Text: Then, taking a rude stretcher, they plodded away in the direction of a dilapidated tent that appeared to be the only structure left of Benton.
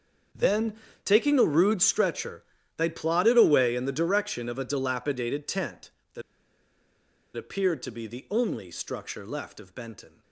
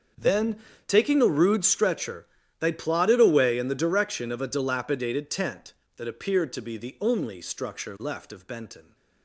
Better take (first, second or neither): second